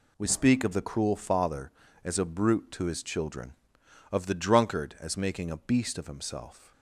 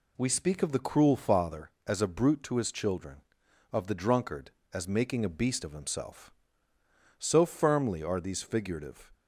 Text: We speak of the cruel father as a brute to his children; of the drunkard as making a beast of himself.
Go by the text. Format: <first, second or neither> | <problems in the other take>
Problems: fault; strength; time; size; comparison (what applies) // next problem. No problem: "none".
first | goes on to say "So firmly are these figurative"; strong; from 7.1 s on; 1.9 s long